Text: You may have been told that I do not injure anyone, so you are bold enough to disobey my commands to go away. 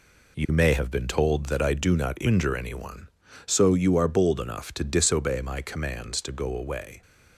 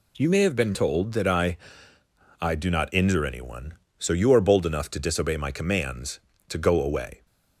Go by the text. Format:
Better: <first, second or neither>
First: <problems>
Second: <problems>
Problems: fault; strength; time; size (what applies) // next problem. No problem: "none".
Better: first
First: none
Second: says "I" twice; at 2.3 s